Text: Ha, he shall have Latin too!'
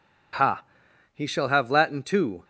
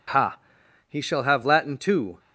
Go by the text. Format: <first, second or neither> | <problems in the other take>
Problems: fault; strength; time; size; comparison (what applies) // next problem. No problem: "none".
neither | none